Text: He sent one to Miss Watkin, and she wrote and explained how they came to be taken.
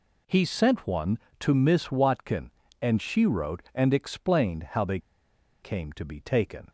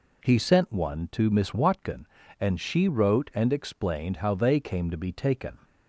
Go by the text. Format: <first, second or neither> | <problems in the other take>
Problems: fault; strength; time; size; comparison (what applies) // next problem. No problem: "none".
second | pauses between "they" and "came"; noticeable; at 4.9 s; 0.63 s long